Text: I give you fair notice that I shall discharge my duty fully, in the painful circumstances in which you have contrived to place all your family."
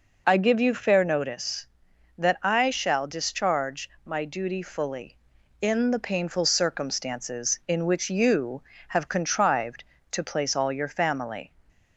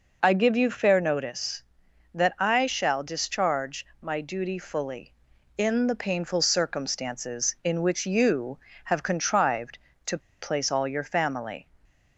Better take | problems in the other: first | pauses between "discharge" and "my"; slight; at 3.8 s; 0.16 s long; slight in the first // pauses between "to" and "place"; slight; at 10.1 s; 0.23 s long

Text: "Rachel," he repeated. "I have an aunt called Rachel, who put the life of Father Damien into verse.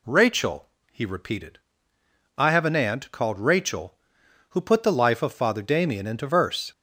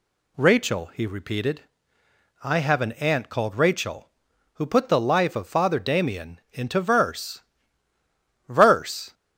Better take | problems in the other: first | says "verse" twice; at 8.4 s

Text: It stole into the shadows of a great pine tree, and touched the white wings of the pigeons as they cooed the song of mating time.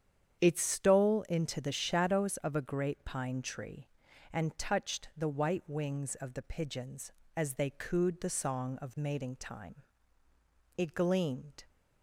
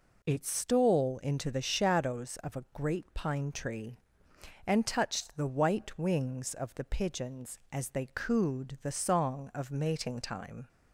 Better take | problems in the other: second | starts louder than the rest; strong; until 1.4 s; 8.5 dB // goes on to say "It gleamed"; noticeable; from 10.7 s on; 0.86 s long

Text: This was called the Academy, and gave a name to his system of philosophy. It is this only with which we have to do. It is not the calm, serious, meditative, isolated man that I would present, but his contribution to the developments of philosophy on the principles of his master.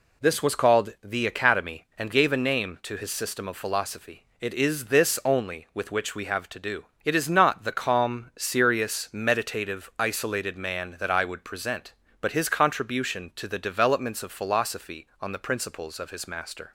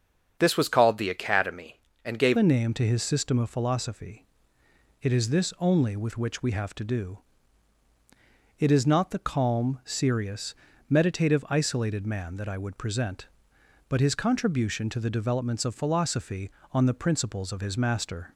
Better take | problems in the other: first | starts louder than the rest; strong; until 1.4 s; 7.5 dB // changes voice at "a"; from 2.3 s on; 16.0 s long

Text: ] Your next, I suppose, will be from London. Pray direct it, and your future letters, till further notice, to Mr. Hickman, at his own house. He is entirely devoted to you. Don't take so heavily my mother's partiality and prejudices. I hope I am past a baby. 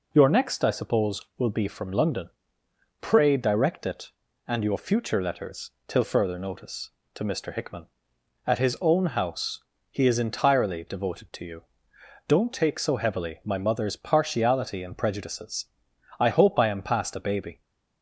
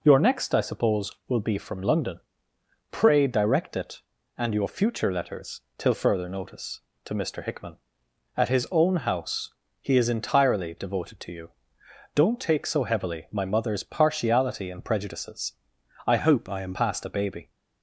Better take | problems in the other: first | changes voice from "hope" to "am"; from 16.1 to 16.7 s; 0.6 s long

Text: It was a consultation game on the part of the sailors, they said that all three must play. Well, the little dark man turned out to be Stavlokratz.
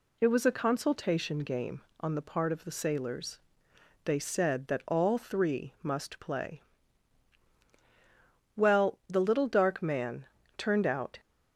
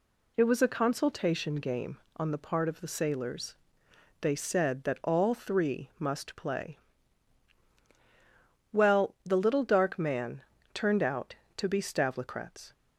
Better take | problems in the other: second | pauses between "man" and "turned"; slight; at 10.2 s; 0.30 s long; slight in the second // stops before "to be Stavlokratz"; at 11.1 s

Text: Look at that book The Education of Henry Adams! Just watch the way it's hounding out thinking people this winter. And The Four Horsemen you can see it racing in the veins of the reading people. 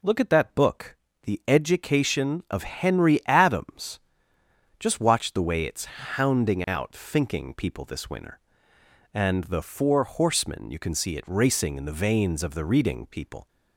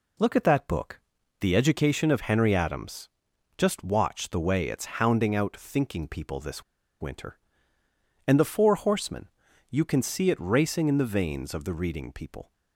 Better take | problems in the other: first | pauses between "book" and "The"; at 0.9 s; 0.42 s long; slight in the first // pauses between "this" and "winter"; at 6.6 s; 0.37 s long // pauses between "Horsemen" and "you"; at 9.2 s; 0.40 s long

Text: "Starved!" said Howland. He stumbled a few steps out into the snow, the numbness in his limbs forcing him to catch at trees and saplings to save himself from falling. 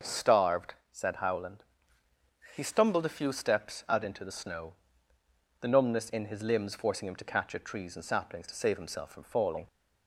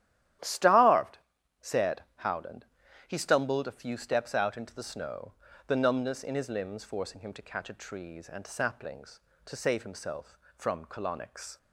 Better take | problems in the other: first | starts louder than the rest; strong; until 1.8 s; 12 dB // says "colonics" for "falling"; at 10.8 s

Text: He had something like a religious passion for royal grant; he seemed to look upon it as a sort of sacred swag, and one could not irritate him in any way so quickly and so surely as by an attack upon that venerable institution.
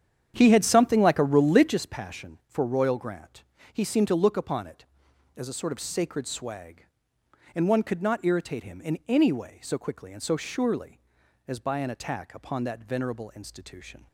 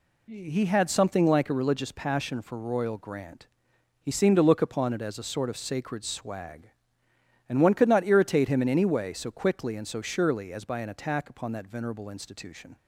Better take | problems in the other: second | starts louder than the rest; strong; until 1.8 s; 9 dB

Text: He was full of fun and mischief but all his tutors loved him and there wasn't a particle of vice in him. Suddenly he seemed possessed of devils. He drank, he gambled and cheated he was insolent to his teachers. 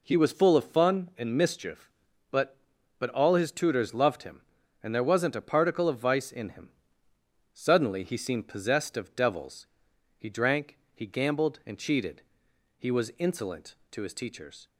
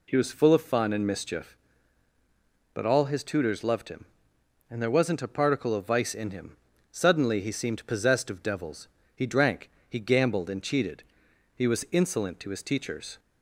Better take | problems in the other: second | says "but" twice; at 2.9 s // pauses between "cheated" and "he"; noticeable; at 12.2 s; 0.56 s long; noticeable in the second

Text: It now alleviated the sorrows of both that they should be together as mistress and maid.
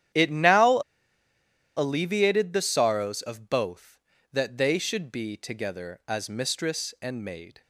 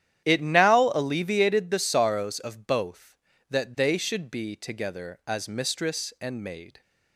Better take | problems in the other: second | starts louder than the rest; strong; until 2.1 s; 11 dB; strong in the second // pauses between "now" and "alleviated"; at 0.7 s; 0.99 s long

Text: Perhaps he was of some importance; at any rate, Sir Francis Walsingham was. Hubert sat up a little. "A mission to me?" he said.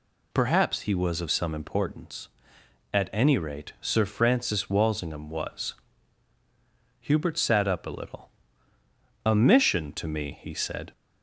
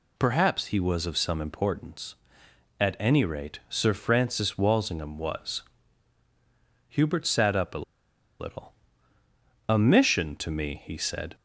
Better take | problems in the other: first | pauses between "a" and "little"; noticeable; at 7.8 s; 0.55 s long

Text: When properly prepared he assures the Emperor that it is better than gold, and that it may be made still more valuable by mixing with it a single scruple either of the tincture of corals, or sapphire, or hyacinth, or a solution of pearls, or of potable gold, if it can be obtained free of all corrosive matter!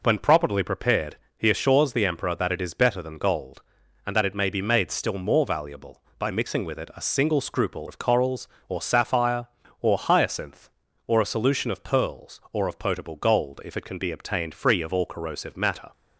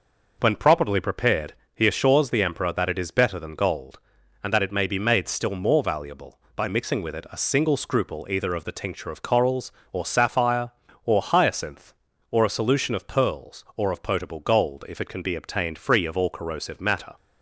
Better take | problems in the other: second | pauses between "prepared" and "he"; slight; at 1.1 s; 0.22 s long; slight in the second // skips "either of the tincture"; at 7.8 s

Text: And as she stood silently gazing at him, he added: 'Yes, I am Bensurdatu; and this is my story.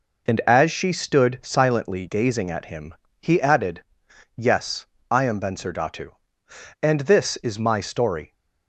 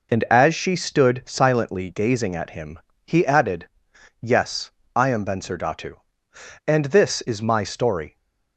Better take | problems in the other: neither | none

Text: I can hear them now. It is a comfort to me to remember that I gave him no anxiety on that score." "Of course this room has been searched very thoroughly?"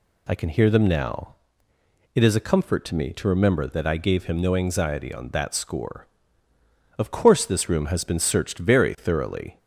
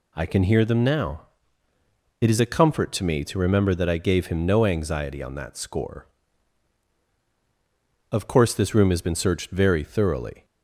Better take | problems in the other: neither | none

